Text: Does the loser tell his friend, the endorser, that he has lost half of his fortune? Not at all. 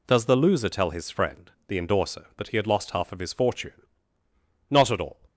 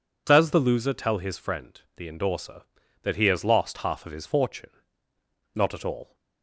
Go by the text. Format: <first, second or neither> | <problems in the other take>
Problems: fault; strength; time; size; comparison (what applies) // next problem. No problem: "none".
second | says "had" for "has"; at 2.5 s